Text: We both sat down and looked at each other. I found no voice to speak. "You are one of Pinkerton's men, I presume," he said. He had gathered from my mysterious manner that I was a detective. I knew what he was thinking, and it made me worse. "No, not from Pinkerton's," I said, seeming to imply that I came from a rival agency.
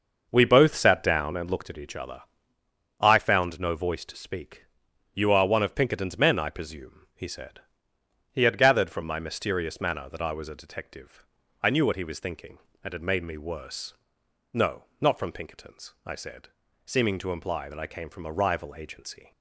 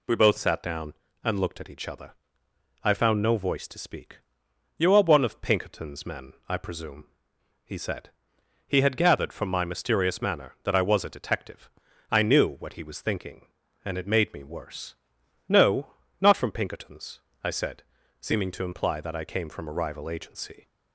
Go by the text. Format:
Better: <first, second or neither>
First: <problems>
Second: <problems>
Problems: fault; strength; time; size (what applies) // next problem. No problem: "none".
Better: second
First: starts louder than the rest; noticeable; until 1.9 s; 6 dB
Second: none